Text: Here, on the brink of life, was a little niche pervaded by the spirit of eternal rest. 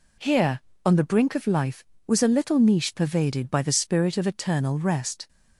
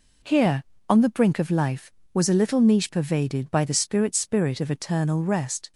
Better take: first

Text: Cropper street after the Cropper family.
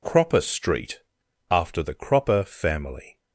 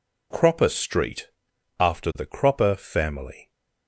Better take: neither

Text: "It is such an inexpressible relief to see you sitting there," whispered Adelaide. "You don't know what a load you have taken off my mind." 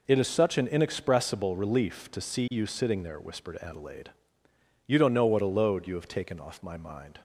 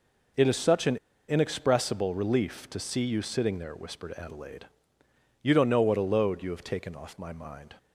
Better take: first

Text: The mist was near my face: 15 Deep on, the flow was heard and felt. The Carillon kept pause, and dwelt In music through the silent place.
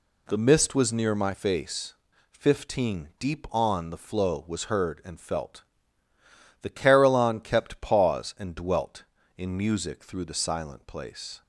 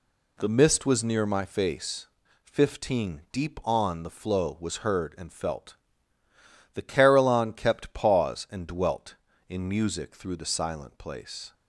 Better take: neither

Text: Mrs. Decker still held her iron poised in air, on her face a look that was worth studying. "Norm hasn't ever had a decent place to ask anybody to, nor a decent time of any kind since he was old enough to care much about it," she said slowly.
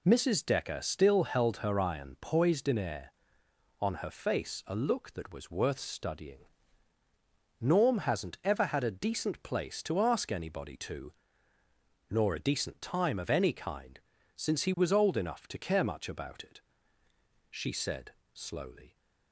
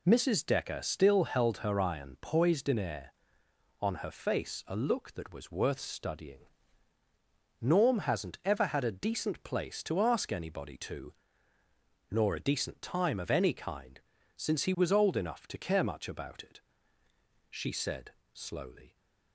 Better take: neither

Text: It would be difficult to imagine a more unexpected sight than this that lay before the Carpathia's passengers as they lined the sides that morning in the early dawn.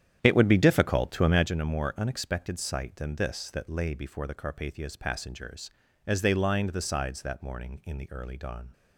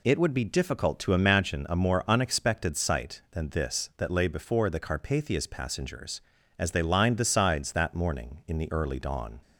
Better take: second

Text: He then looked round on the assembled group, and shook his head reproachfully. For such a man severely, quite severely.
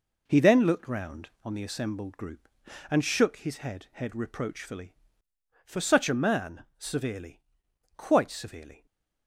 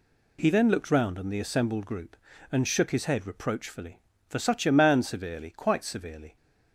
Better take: second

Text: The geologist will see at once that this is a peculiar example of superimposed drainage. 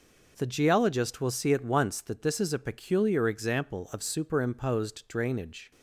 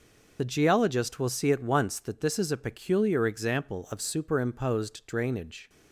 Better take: first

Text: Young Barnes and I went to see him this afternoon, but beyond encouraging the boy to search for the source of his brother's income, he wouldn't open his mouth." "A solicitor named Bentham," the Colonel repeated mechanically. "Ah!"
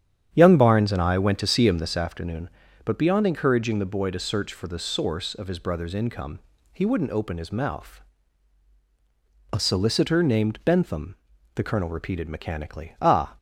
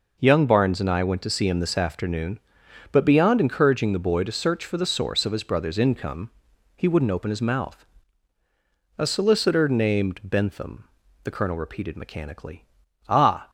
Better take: second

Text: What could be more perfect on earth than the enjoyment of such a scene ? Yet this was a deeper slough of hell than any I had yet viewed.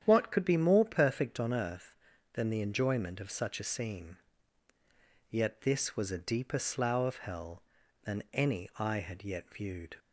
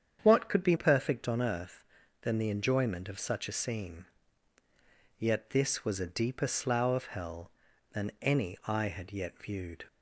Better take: first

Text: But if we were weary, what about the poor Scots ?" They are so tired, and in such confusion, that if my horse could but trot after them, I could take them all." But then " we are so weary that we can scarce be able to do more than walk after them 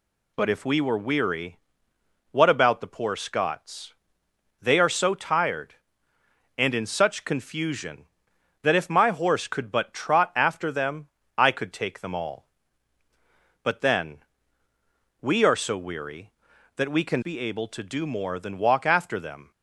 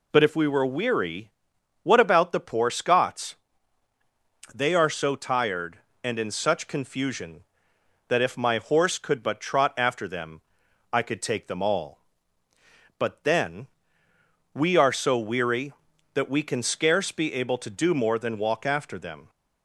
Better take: second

